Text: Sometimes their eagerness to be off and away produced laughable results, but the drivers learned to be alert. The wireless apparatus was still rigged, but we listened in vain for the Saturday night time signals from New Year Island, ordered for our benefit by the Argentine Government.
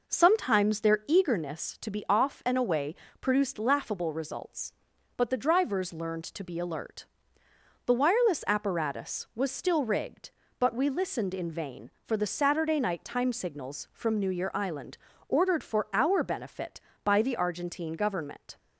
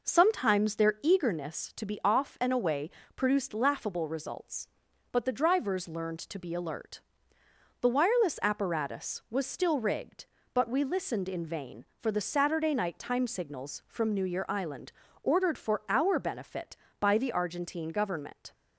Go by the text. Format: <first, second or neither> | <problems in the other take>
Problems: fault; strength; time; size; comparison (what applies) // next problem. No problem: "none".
neither | pauses between "away" and "produced"; slight; the same in both